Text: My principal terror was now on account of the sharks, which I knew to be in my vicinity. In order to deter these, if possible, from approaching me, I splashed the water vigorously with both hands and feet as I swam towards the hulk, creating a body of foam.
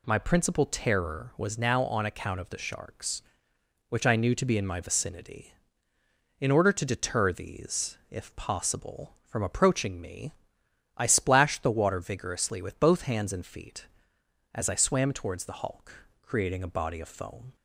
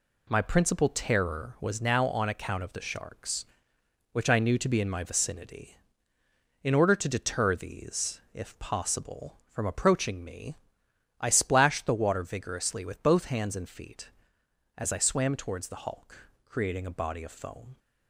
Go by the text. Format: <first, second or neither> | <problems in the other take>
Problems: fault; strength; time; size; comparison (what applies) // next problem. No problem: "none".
first | gets quieter; throughout; 7 dB